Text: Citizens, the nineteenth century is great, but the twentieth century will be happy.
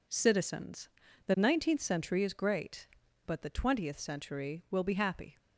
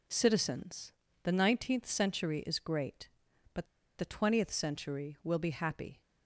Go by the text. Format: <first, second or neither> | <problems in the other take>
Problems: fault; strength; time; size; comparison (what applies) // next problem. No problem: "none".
first | pauses between "but" and "the"; slight; at 3.6 s; 0.32 s long